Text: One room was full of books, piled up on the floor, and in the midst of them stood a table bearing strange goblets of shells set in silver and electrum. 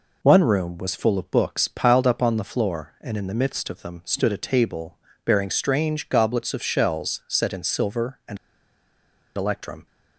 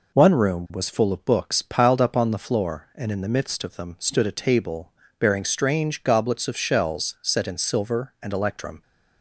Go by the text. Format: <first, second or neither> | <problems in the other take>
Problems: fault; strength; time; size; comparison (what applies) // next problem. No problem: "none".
second | pauses between "table" and "bearing"; slight; at 4.9 s; 0.26 s long; slight in the second // pauses between "and" and "electrum"; at 8.3 s; 0.98 s long